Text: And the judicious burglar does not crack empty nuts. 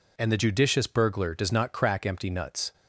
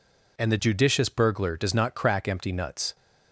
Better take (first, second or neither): neither